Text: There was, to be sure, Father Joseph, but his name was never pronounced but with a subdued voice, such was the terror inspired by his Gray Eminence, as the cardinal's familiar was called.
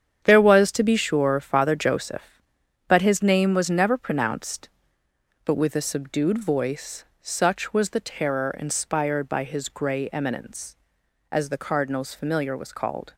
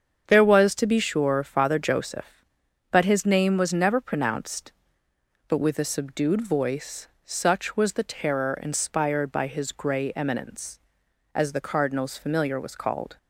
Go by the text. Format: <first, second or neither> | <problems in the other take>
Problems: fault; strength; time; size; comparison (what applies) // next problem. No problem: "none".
second | gets quieter; strong; throughout; 9.5 dB // starts louder than the rest; strong; until 1.2 s; 8.5 dB; strong in the second